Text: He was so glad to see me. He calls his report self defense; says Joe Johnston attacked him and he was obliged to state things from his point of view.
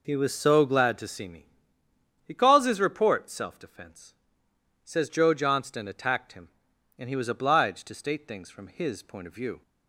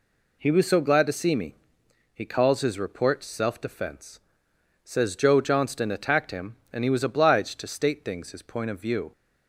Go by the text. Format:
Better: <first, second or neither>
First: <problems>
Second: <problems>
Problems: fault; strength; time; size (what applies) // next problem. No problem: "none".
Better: first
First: none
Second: skips "from"; at 8.3 s